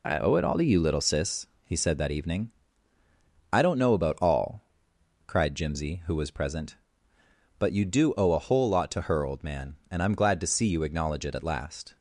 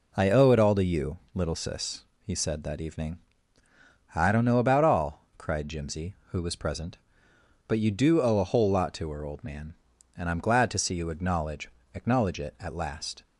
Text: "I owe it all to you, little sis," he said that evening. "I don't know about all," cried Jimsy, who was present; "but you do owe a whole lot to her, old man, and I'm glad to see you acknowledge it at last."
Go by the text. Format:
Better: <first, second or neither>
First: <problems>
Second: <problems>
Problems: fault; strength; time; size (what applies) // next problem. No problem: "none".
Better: first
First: none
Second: says "acknowledge" twice; at 11.9 s